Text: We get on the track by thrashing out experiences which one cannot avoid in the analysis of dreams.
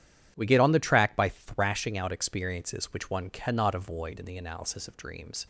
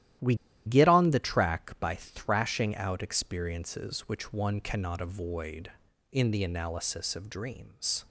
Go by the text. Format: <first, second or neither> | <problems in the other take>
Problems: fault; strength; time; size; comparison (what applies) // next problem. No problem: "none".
first | starts louder than the rest; strong; until 1.5 s; 12.5 dB; strong in the first // pauses between "We" and "get"; slight; at 0.3 s; 0.31 s long